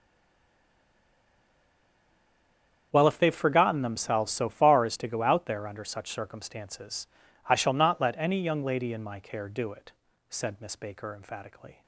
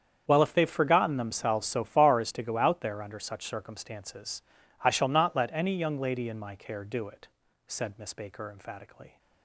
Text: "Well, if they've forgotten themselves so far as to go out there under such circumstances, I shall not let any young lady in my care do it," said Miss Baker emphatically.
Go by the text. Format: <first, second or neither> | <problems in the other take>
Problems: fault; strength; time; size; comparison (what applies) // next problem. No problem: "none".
second | stays silent before the first word; strong; until 2.9 s; 2.9 s long // starts louder than the rest; strong; until 3.9 s; 8 dB; strong in the second